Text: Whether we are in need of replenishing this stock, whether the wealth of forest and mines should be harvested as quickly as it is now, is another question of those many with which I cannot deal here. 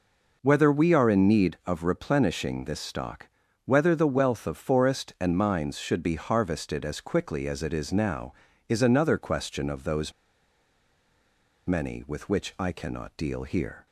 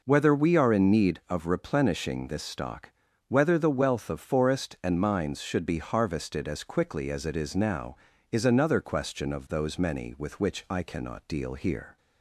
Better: second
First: pauses between "those" and "many"; strong; at 10.1 s; 1.5 s long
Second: none

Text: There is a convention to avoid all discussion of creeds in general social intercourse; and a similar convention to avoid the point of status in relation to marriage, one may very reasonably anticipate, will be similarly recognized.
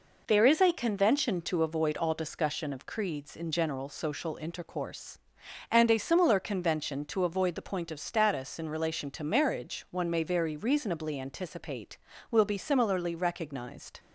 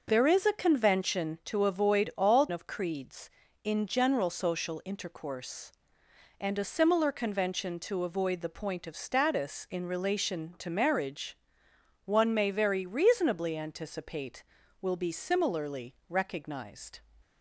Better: first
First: none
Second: skips "discussion"; at 2.4 s // pauses between "similarly" and "recognized"; slight; at 15.9 s; 0.16 s long

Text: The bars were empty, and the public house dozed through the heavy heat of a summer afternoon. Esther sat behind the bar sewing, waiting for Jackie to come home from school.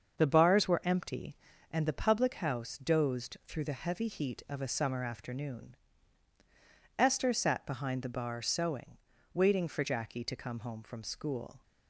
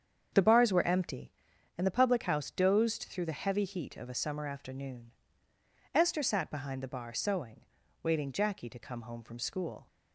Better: first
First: starts louder than the rest; until 1.2 s; 7 dB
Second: starts louder than the rest; strong; until 1.8 s; 7.5 dB // skips "for"; at 8.3 s

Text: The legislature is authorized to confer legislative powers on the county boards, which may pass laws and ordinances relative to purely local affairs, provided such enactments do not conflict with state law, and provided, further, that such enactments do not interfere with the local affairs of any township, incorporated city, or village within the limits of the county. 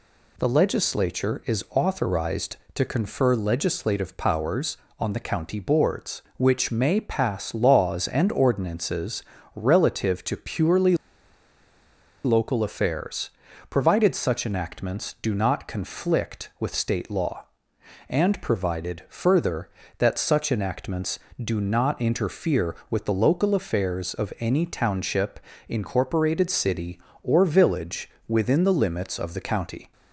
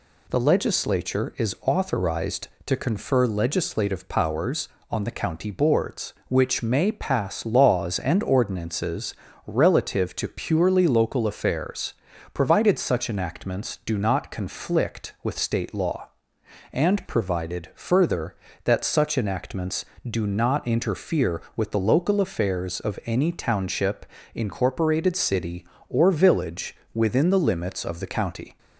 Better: second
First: pauses between "ordinances" and "relative"; slight; at 9.2 s; 0.32 s long // pauses between "purely" and "local"; strong; at 10.9 s; 1.2 s long // pauses between "village" and "within"; slight; at 28.0 s; 0.16 s long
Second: pauses between "ordinances" and "relative"; slight; at 9.1 s; 0.32 s long // pauses between "village" and "within"; slight; at 26.7 s; 0.16 s long

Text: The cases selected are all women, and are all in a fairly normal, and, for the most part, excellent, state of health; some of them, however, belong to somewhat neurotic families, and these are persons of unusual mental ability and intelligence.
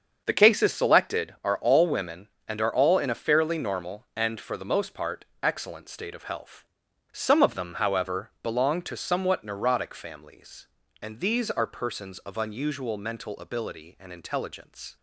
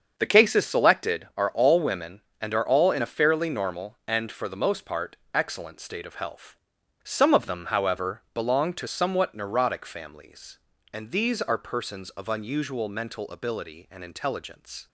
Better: neither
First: starts louder than the rest; until 1.2 s; 7 dB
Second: starts louder than the rest; until 1.1 s; 7 dB

